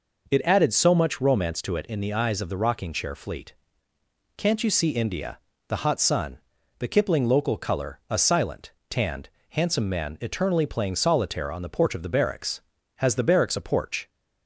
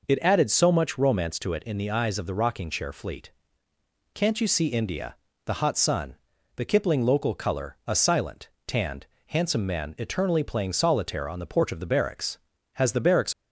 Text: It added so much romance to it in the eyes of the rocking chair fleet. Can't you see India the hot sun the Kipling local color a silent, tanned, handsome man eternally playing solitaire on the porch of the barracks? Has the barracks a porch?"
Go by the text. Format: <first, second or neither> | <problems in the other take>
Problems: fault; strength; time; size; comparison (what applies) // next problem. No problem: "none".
first | pauses between "India" and "the"; slight; at 5.1 s; 0.30 s long; slight in the first // pauses between "sun" and "the"; at 6.1 s; 0.40 s long; also in the first // stops before "a porch"; at 13.3 s